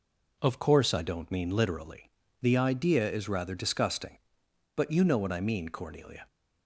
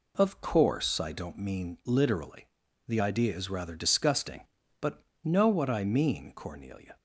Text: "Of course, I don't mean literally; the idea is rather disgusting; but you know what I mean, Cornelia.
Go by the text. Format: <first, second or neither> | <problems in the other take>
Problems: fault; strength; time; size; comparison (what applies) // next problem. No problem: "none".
first | skips "you"; at 5.1 s